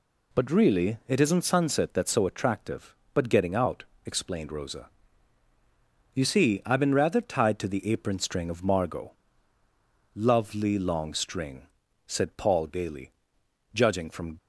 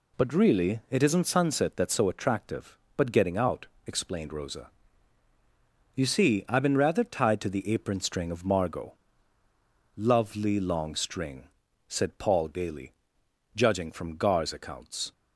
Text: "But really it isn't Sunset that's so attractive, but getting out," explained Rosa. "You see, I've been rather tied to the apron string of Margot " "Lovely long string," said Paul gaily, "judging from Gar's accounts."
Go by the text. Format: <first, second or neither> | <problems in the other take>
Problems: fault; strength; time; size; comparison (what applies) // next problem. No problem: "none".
second | stops before "Gar's accounts"; at 14.3 s